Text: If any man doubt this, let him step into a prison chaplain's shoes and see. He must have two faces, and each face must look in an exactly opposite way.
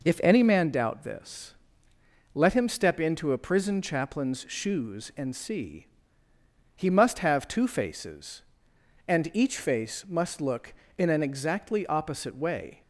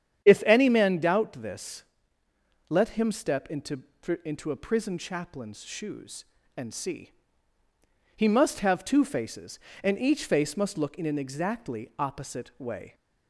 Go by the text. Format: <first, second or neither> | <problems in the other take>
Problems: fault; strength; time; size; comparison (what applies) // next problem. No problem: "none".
first | starts louder than the rest; strong; until 1.2 s; 9 dB // says "into" twice; at 4.2 s